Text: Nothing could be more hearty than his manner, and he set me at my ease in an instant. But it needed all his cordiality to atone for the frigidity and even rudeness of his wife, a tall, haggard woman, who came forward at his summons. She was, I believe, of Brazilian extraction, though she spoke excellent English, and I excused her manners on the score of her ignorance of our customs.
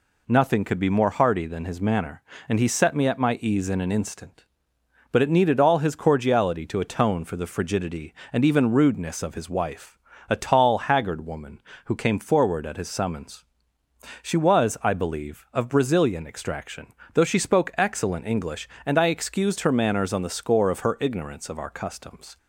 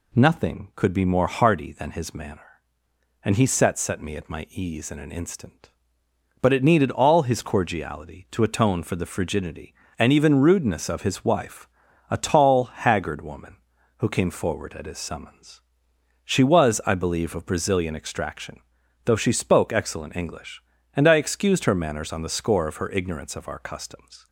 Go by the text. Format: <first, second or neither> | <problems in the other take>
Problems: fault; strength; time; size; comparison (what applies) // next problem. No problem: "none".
first | says "set" twice; at 3.7 s